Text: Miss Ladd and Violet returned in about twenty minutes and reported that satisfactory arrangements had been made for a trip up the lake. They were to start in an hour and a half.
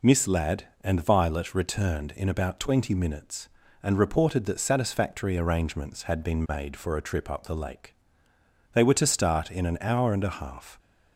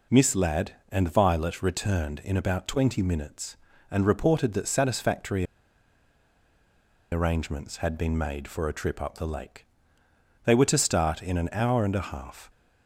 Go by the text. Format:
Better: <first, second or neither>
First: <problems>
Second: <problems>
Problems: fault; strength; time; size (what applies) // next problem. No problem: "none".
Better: first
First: none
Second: pauses between "satisfactory" and "arrangements"; strong; at 5.4 s; 1.6 s long